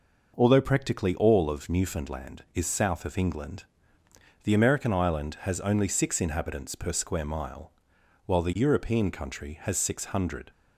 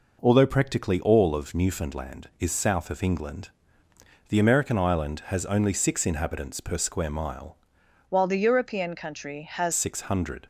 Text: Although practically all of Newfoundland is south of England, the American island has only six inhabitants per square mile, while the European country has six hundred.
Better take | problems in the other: first | changes voice from "while" to "has"; from 8.0 to 9.7 s; 1.7 s long

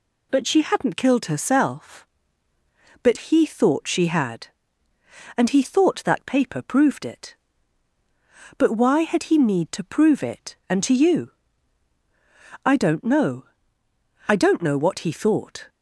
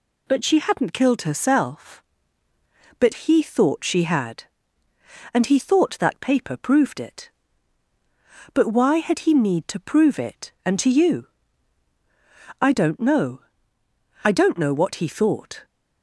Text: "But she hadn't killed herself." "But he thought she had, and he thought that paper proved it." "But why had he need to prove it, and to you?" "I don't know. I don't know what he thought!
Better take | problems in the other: neither | none

